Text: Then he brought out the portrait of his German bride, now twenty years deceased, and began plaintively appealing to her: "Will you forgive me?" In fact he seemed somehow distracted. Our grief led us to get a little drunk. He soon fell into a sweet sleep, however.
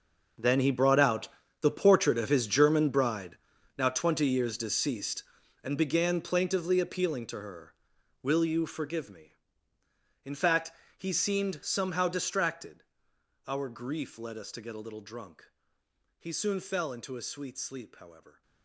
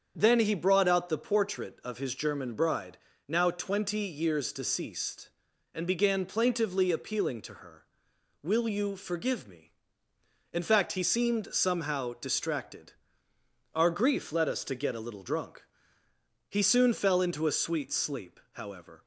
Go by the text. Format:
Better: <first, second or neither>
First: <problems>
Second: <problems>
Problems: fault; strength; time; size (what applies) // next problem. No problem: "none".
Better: second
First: gets quieter; strong; throughout; 15.5 dB // starts louder than the rest; noticeable; until 1.7 s; 6 dB // pauses between "out" and "the"; slight; at 1.2 s; 0.32 s long // pauses between "fact" and "he"; slight; at 10.7 s; 0.26 s long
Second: starts louder than the rest; strong; until 1.1 s; 7 dB